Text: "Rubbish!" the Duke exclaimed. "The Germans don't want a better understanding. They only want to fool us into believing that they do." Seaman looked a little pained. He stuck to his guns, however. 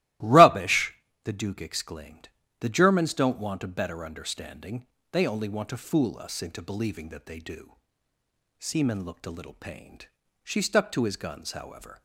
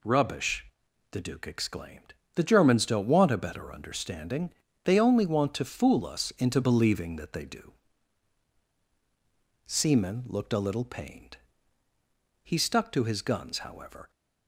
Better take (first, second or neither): second